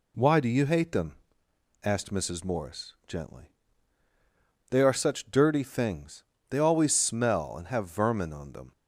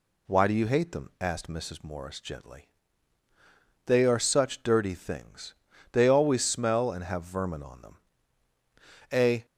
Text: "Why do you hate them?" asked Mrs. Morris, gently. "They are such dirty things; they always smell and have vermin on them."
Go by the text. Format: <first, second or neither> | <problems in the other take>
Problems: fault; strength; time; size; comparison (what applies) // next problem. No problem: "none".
first | goes on to say "A"; slight; from 9.1 s on; 0.32 s long